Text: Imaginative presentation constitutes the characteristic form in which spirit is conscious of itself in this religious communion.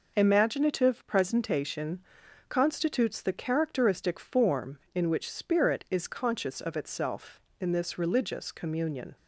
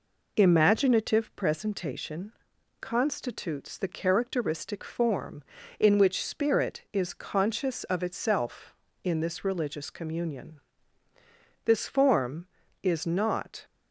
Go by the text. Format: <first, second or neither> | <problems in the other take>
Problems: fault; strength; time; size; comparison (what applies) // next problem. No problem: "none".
first | pauses between "presentation" and "constitutes"; noticeable; at 2.3 s; 0.48 s long; noticeable in the first // goes on to say "This form is not"; strong; from 11.6 s on; 2.0 s long